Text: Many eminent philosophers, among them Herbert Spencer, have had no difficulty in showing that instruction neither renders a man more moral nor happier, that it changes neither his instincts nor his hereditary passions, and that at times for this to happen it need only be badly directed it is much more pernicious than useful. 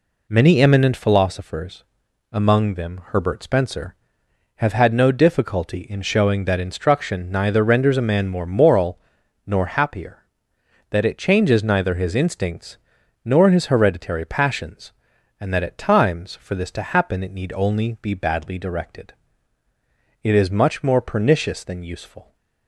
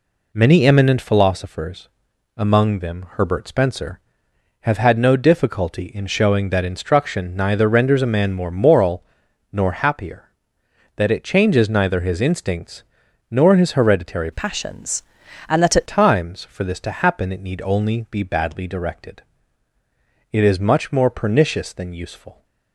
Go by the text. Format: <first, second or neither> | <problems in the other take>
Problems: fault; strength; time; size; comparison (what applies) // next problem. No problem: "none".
first | pauses between "moral" and "nor"; noticeable; at 9.0 s; 0.50 s long; noticeable in the first // pauses between "instincts" and "nor"; noticeable; at 12.8 s; 0.48 s long; noticeable in the first // changes voice from "passions" to "at"; from 14.3 to 15.8 s; 1.5 s long // pauses between "directed" and "it"; at 19.2 s; 1.1 s long; also in the first